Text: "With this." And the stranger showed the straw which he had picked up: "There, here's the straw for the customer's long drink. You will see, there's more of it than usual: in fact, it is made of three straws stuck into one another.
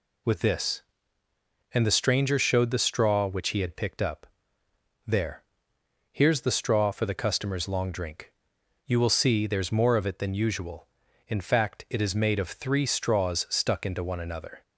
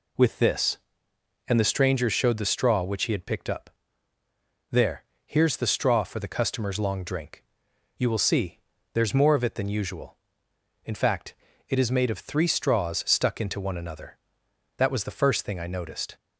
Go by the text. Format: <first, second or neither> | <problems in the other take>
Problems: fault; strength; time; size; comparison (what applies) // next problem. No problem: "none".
first | goes on to say "That was the first thing I noticed"; from 14.7 s on; 1.3 s long